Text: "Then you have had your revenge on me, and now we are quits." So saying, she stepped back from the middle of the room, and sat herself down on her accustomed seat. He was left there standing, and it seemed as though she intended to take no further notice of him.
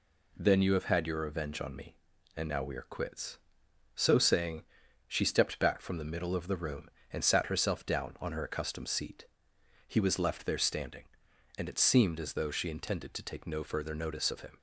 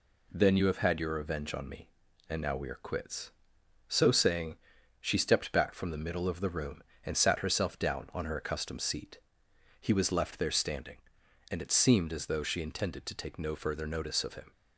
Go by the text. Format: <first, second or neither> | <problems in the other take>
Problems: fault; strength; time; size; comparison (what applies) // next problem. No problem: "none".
neither | none